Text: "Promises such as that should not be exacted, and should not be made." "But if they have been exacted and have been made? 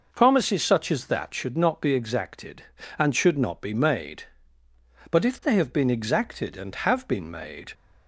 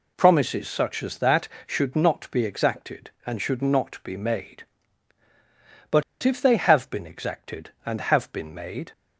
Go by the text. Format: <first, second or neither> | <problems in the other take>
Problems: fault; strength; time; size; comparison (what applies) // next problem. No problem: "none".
first | pauses between "But" and "if"; slight; at 6.0 s; 0.20 s long